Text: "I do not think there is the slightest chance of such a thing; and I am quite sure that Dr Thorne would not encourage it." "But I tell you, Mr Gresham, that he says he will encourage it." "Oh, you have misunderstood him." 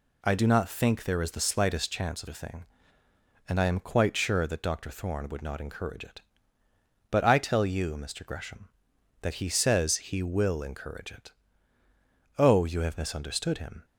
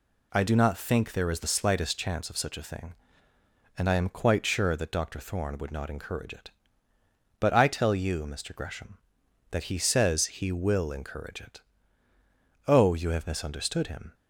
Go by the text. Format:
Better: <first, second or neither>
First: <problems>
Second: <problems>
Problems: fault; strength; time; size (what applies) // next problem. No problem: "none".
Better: second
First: skips "such"; at 2.2 s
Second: none